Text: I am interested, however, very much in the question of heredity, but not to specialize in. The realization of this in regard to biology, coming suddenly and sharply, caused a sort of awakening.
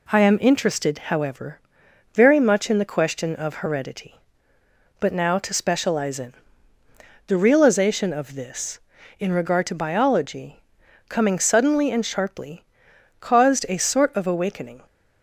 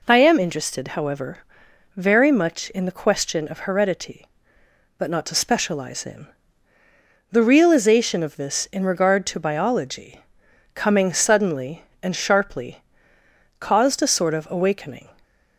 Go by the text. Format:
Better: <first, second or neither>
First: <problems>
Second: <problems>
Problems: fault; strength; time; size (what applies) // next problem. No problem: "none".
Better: second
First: says "now" for "not"; at 5.1 s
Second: none